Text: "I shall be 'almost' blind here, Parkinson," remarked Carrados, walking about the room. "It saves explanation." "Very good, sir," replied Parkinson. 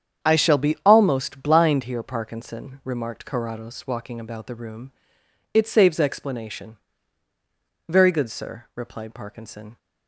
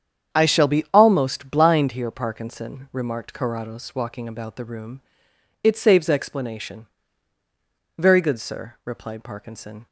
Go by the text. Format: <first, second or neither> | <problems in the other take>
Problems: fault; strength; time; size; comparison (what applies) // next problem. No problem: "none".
neither | starts louder than the rest; strong; the same in both